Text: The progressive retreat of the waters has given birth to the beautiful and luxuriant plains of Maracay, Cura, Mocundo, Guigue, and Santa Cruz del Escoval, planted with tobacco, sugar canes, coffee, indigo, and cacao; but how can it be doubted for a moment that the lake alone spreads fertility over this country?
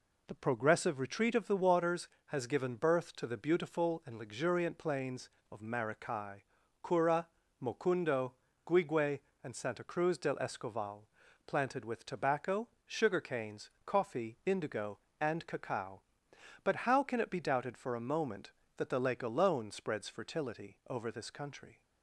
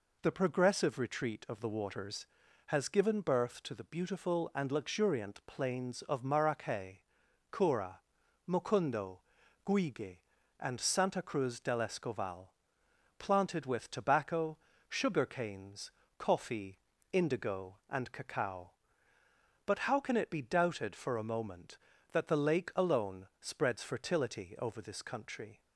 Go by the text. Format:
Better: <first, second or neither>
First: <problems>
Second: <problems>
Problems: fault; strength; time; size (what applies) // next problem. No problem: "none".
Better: neither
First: none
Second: none